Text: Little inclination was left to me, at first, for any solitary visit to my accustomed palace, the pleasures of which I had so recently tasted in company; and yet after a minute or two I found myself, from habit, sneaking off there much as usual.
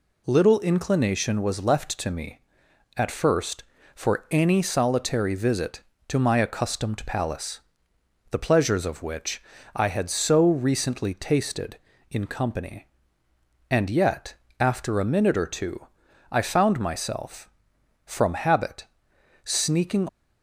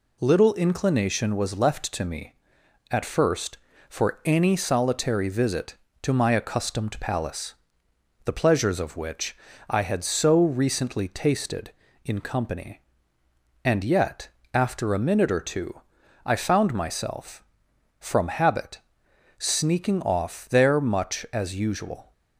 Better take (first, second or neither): second